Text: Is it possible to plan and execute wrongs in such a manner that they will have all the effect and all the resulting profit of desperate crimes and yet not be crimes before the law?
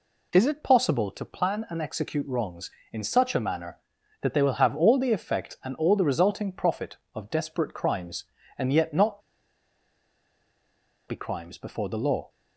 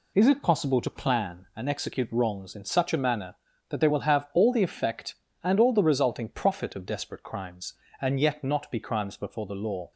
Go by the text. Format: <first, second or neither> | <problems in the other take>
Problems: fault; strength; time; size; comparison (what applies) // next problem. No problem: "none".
second | pauses between "not" and "be"; strong; at 9.2 s; 1.8 s long